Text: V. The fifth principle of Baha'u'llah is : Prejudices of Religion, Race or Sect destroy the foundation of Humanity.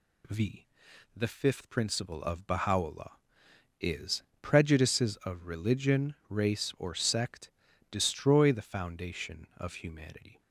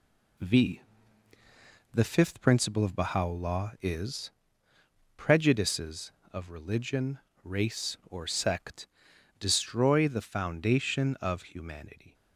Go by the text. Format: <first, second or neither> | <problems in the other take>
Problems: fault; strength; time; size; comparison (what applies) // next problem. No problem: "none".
first | gets quieter; noticeable; throughout; 4.5 dB // pauses between "Sect" and "destroy"; noticeable; at 8.8 s; 0.52 s long; also in the first